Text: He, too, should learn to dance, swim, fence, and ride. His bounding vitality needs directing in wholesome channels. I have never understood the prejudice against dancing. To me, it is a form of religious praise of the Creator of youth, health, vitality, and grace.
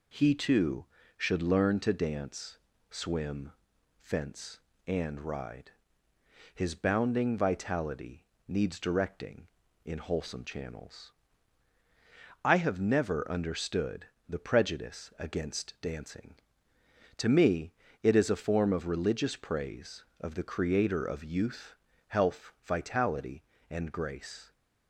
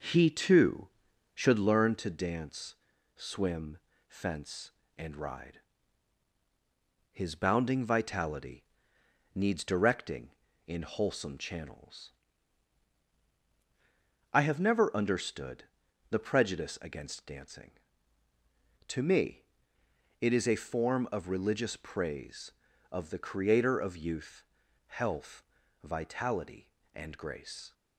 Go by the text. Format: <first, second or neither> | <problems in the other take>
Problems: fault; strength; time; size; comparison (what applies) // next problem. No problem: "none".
first | starts louder than the rest; noticeable; until 1.7 s; 6 dB // pauses between "vitality" and "needs"; noticeable; at 8.6 s; 0.72 s long; slight in the first // pauses between "understood" and "the"; at 15.6 s; 0.44 s long; slight in the first